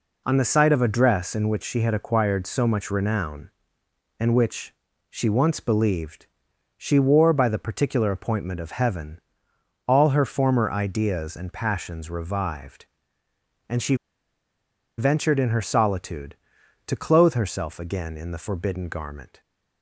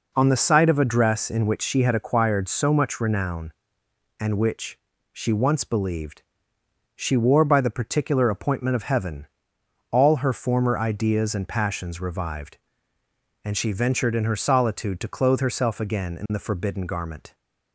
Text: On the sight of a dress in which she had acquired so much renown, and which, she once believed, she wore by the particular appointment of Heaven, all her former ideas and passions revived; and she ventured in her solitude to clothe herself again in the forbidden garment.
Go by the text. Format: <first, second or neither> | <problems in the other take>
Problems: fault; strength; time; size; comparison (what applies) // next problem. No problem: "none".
second | pauses between "she" and "ventured"; at 13.9 s; 1.0 s long